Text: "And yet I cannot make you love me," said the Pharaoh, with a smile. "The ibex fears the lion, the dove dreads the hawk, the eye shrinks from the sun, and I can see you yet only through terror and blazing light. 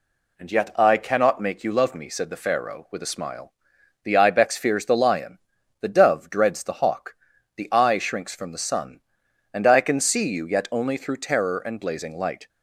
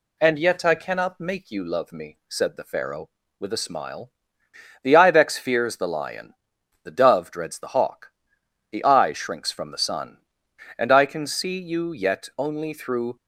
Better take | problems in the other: first | stops before "terror and blazing light"; at 13.1 s

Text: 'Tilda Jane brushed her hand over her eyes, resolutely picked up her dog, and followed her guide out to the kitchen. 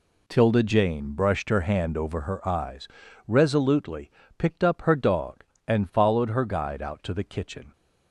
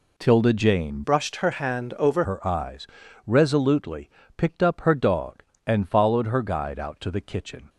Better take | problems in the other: first | changes voice from "brushed" to "over"; from 1.0 to 2.2 s; 1.2 s long // pauses between "resolutely" and "picked"; slight; at 4.0 s; 0.28 s long; slight in the first

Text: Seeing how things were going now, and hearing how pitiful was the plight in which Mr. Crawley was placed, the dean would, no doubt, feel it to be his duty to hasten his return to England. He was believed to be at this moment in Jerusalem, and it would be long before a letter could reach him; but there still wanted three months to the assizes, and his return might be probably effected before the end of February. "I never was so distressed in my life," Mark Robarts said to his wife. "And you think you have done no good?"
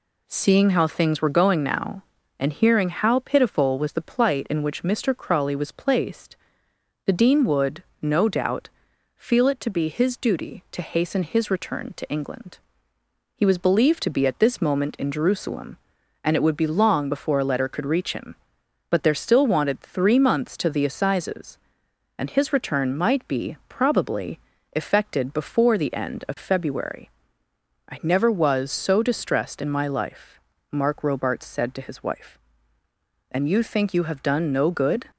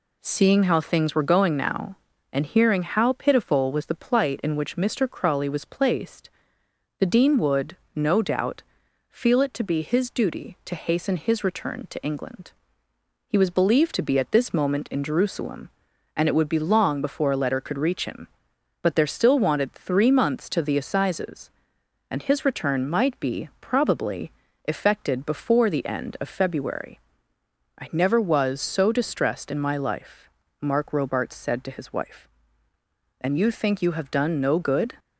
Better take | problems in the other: neither | pauses between "probably" and "effected"; slight; the same in both

